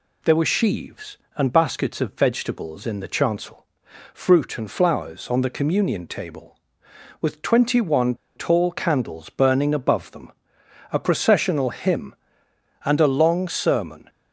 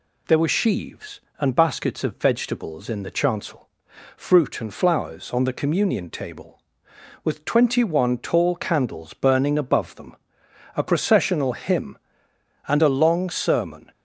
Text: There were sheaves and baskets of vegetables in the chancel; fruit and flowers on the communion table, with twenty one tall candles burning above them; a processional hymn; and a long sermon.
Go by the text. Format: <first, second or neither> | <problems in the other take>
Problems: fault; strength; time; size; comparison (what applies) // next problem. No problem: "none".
second | pauses between "one" and "tall"; slight; at 8.1 s; 0.21 s long